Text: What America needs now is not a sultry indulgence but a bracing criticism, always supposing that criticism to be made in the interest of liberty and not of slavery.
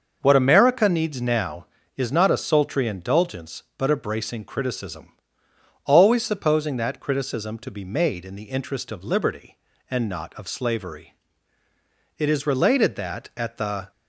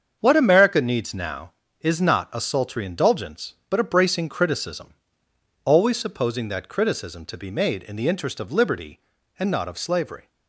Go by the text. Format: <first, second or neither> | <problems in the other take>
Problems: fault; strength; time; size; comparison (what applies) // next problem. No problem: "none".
second | starts louder than the rest; until 1.2 s; 6.5 dB; strong in the second // goes on to say "It is related that at the"; strong; from 12.1 s on; 1.7 s long